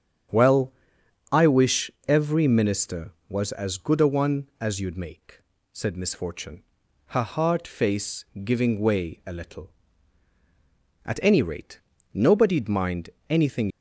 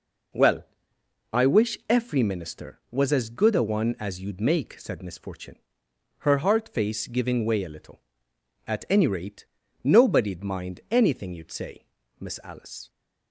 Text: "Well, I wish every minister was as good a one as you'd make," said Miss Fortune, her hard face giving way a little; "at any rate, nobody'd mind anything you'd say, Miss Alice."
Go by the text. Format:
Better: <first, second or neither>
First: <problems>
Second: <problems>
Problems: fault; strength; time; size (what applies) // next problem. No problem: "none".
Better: second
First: starts louder than the rest; strong; until 1.9 s; 8 dB // pauses between "wish" and "every"; slight; at 1.9 s; 0.16 s long // pauses between "face" and "giving"; slight; at 8.2 s; 0.20 s long // pauses between "mind" and "anything"; slight; at 13.0 s; 0.20 s long // stops before "you'd say Miss Alice"; at 13.6 s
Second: none